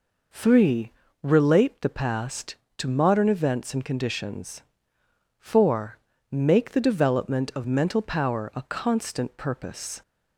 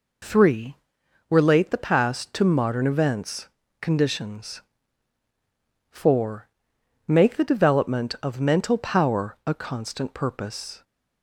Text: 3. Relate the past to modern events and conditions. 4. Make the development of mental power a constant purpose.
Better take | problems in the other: first | skips "and"; at 3.6 s

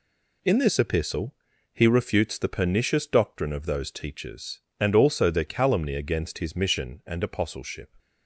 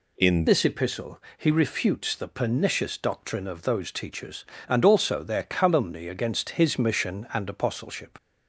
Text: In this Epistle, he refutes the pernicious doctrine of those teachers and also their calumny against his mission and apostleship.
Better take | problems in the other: first | changes voice at "this"; from 0.4 s on; 7.7 s long

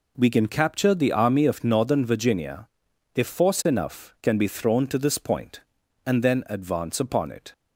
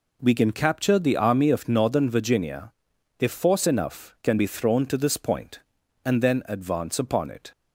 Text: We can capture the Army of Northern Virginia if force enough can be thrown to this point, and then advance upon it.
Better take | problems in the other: neither | pauses between "Virginia" and "if"; noticeable; the same in both

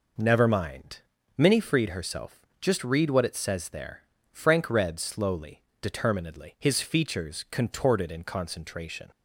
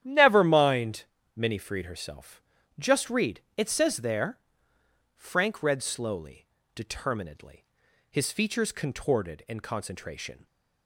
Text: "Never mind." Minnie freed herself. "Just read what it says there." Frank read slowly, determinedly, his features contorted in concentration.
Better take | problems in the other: first | starts louder than the rest; strong; until 1.0 s; 11 dB // skips "what"; at 3.4 s

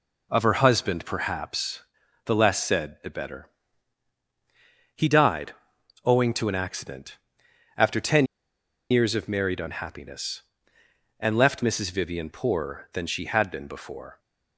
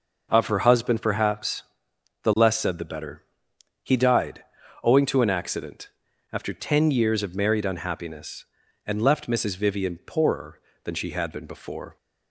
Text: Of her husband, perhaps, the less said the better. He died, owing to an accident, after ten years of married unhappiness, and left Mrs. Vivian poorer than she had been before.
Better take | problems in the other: second | pauses between "ten" and "years"; noticeable; at 8.2 s; 0.64 s long

